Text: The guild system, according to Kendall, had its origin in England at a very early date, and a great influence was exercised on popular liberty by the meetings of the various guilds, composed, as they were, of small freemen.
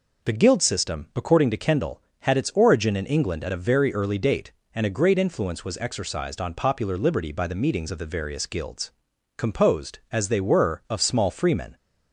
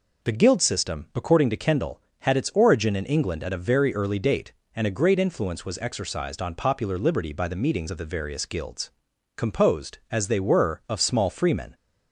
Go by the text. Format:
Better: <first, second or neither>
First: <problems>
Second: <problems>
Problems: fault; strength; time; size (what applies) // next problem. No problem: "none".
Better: neither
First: none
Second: none